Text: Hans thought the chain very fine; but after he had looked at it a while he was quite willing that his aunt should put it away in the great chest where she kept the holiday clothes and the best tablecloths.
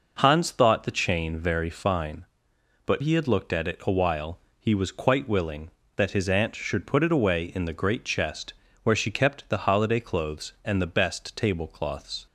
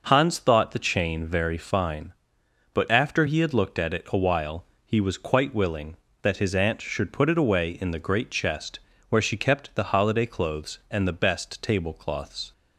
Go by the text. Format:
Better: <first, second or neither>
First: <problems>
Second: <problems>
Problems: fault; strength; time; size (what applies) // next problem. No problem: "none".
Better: second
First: skips "after"; at 3.0 s // pauses between "while" and "he"; slight; at 4.3 s; 0.18 s long // pauses between "chest" and "where"; slight; at 8.5 s; 0.28 s long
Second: pauses between "while" and "he"; slight; at 4.6 s; 0.18 s long // pauses between "chest" and "where"; slight; at 8.7 s; 0.28 s long